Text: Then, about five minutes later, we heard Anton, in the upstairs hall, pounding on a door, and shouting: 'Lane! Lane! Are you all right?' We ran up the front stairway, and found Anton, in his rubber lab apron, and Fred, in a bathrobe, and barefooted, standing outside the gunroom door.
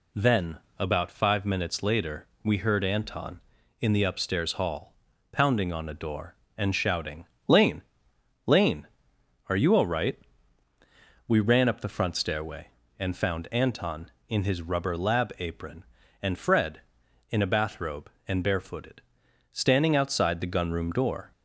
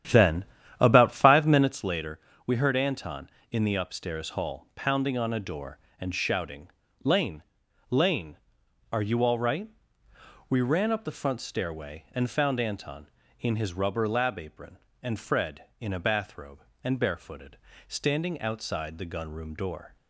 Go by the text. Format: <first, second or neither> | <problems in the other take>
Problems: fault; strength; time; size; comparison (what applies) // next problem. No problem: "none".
first | starts louder than the rest; strong; until 1.9 s; 10.5 dB